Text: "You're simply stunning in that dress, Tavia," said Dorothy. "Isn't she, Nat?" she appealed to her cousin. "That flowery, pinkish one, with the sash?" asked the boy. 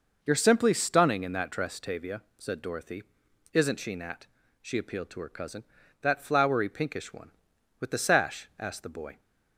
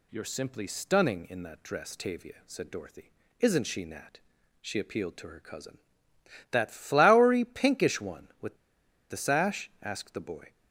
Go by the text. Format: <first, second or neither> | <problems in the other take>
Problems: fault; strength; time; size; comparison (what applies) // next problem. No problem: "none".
first | pauses between "with" and "the"; noticeable; at 8.5 s; 0.53 s long